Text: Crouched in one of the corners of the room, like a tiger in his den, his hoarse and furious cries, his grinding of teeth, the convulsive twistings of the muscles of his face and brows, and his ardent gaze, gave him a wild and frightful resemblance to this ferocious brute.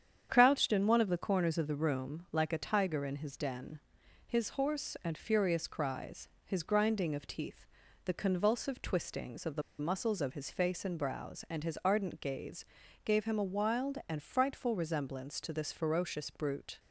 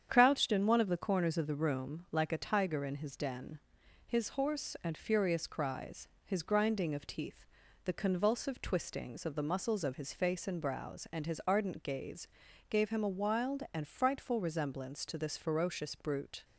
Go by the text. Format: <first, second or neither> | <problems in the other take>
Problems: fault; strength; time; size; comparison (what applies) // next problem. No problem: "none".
second | starts louder than the rest; strong; until 1.3 s; 8.5 dB; strong in the second // pauses between "the" and "muscles"; slight; at 9.6 s; 0.17 s long